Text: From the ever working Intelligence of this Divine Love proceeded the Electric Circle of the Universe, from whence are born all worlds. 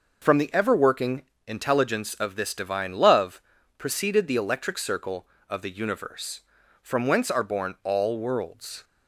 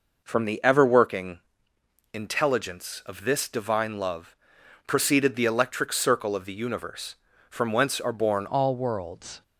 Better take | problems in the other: first | pauses between "working" and "Intelligence"; noticeable; at 1.3 s; 0.74 s long; slight in the first // pauses between "Love" and "proceeded"; noticeable; at 4.3 s; 0.50 s long; slight in the first // changes voice at "all"; from 8.4 s on; 1.0 s long

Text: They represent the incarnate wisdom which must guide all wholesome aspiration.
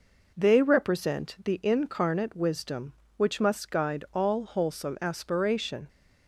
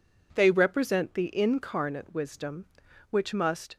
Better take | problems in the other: first | stops before "guide all wholesome aspiration"; at 3.7 s

